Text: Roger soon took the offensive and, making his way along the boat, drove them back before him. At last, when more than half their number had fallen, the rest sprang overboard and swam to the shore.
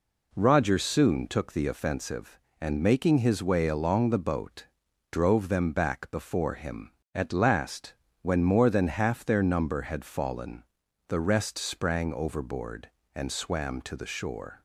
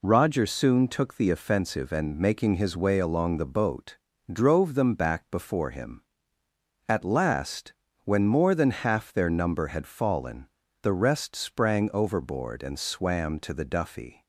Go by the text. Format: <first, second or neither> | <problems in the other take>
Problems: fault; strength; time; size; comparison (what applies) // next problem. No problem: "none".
first | says "duffy" for "shore"; at 13.6 s